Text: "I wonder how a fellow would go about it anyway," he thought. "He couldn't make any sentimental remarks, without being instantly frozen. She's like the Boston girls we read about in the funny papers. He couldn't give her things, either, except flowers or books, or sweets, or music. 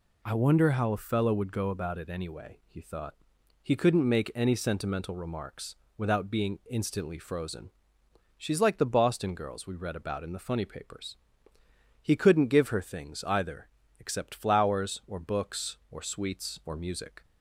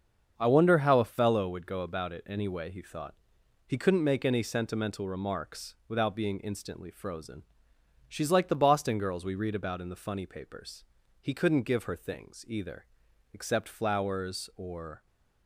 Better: first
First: none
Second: starts louder than the rest; until 1.3 s; 7 dB // stops before "books or sweets or music"; at 15.0 s

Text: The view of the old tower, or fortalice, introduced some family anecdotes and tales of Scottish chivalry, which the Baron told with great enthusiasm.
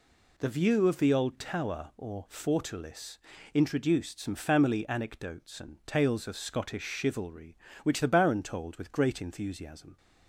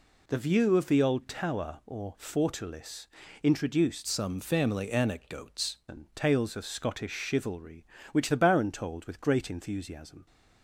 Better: first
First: none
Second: changes voice from "some" to "anecdotes"; from 4.0 to 5.7 s; 1.7 s long

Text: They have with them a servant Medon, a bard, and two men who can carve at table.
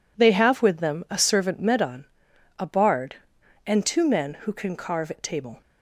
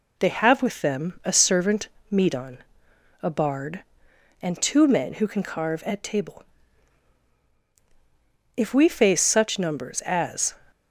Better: first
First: none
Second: pauses between "servant" and "Medon"; slight; at 1.8 s; 0.22 s long // goes on to say "If we face such numbers as"; strong; from 8.5 s on; 2.0 s long

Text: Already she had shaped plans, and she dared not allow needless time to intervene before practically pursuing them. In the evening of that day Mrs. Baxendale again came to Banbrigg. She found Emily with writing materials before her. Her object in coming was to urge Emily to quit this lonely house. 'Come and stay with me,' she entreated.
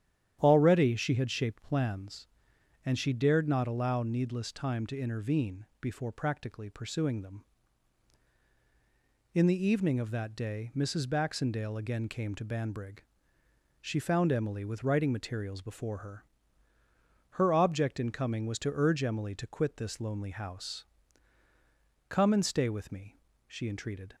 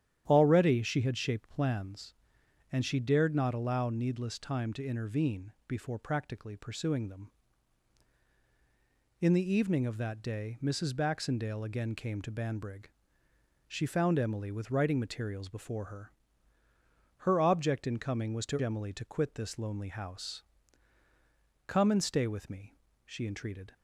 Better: first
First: starts louder than the rest; strong; until 1.4 s; 10.5 dB // pauses between "intervene" and "before"; slight; at 5.6 s; 0.16 s long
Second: starts louder than the rest; strong; until 1.2 s; 10.5 dB // pauses between "intervene" and "before"; slight; at 5.5 s; 0.16 s long // skips "urge"; at 18.5 s

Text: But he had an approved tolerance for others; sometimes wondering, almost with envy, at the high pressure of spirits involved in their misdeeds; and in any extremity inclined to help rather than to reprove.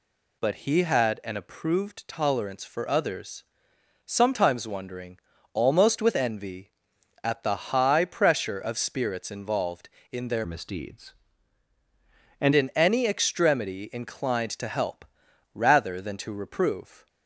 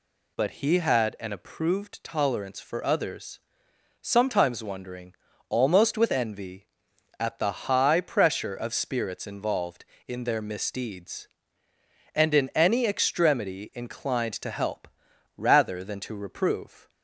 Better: second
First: changes voice from "misdeeds" to "and"; from 10.4 to 12.5 s; 2.1 s long // pauses between "help" and "rather"; noticeable; at 15.0 s; 0.50 s long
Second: pauses between "help" and "rather"; noticeable; at 14.8 s; 0.50 s long

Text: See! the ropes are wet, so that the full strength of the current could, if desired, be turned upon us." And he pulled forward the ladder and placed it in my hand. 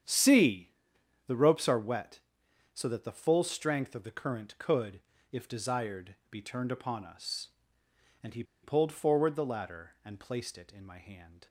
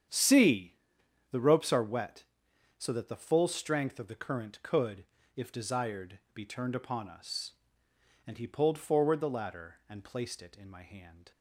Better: second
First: starts louder than the rest; strong; until 1.6 s; 8.5 dB // pauses between "he" and "pulled"; slight; at 8.4 s; 0.20 s long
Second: starts louder than the rest; strong; until 1.6 s; 8.5 dB

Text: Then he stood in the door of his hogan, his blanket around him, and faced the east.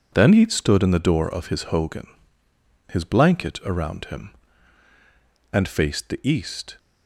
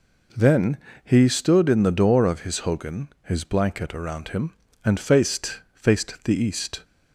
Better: first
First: none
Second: pauses between "Then" and "he"; slight; at 0.7 s; 0.26 s long // says "faced" twice; at 5.7 s

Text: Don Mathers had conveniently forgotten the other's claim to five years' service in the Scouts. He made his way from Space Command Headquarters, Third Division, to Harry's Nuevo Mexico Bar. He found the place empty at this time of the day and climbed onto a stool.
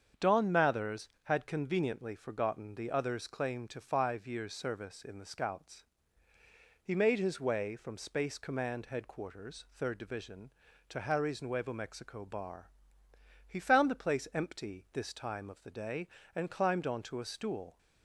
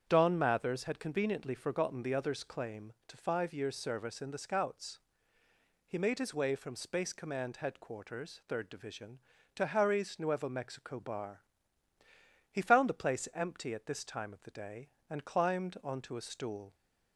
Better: second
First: starts louder than the rest; strong; until 1.3 s; 7.5 dB // skips "at"; at 14.8 s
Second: starts louder than the rest; strong; until 1.0 s; 8 dB

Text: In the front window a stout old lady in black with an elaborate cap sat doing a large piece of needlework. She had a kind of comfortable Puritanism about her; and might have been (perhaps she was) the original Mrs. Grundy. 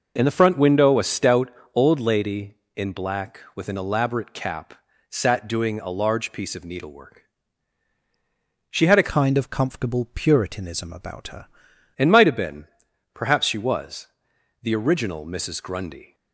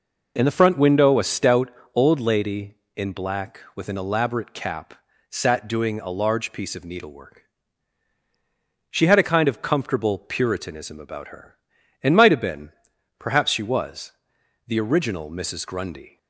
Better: second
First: pauses between "stout" and "old"; slight; at 1.5 s; 0.24 s long // pauses between "cap" and "sat"; at 4.7 s; 0.38 s long // changes voice from "kind" to "her"; from 9.1 to 11.4 s; 2.3 s long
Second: pauses between "stout" and "old"; slight; at 1.7 s; 0.24 s long // pauses between "cap" and "sat"; at 4.9 s; 0.38 s long

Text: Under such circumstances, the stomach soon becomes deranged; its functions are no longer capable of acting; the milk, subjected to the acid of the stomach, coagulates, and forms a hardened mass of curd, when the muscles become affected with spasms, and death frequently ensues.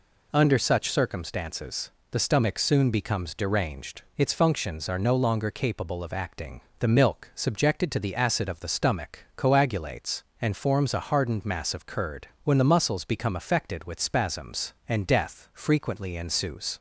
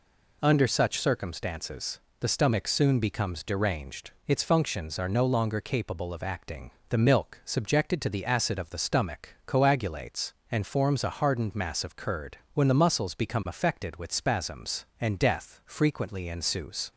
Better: neither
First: none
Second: none

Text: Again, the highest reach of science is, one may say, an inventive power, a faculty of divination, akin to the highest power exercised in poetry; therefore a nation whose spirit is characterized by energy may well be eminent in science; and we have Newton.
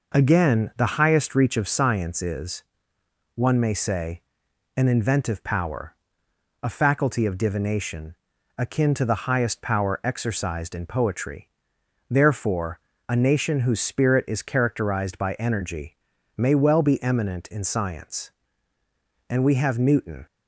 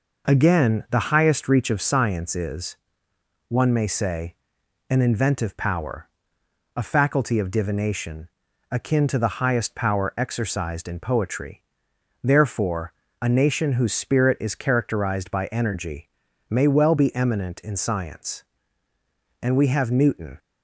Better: neither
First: pauses between "therefore" and "a"; slight; at 12.7 s; 0.30 s long // pauses between "energy" and "may"; at 15.9 s; 0.40 s long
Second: pauses between "therefore" and "a"; slight; at 12.9 s; 0.29 s long // pauses between "energy" and "may"; at 16.0 s; 0.40 s long

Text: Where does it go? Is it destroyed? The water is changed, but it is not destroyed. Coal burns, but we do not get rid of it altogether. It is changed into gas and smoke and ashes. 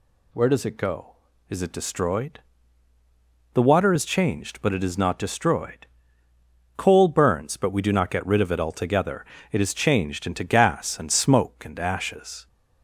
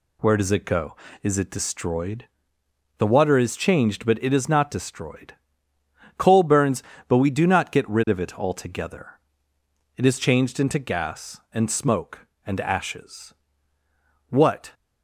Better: first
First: none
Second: goes on to say "What"; slight; from 14.2 s on; 0.44 s long

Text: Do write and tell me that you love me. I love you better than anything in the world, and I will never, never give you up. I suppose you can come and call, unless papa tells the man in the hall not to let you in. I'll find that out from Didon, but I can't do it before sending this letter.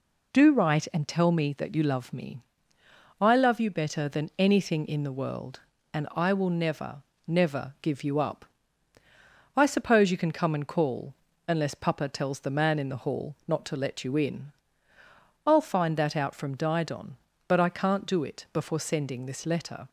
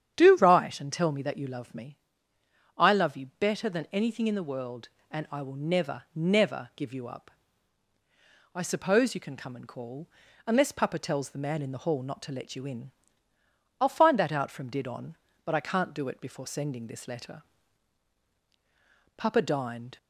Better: first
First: none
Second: starts louder than the rest; strong; until 1.1 s; 9 dB // goes on to say "Papa dined"; noticeable; from 19.1 s on; 0.80 s long

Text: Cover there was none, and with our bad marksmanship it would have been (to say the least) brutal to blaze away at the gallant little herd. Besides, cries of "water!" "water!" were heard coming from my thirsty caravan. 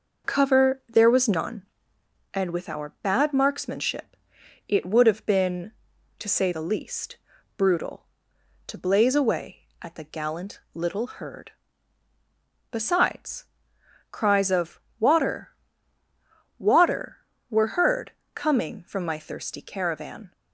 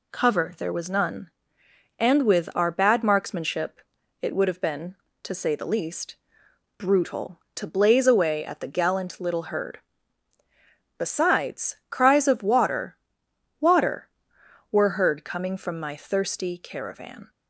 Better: second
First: starts louder than the rest; noticeable; until 2.1 s; 5.5 dB // pauses between "marksmanship" and "it"; noticeable; at 4.1 s; 0.52 s long // pauses between "of" and "water"; slight; at 14.7 s; 0.18 s long // pauses between "heard" and "coming"; slight; at 18.1 s; 0.24 s long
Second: pauses between "marksmanship" and "it"; at 3.7 s; 0.42 s long

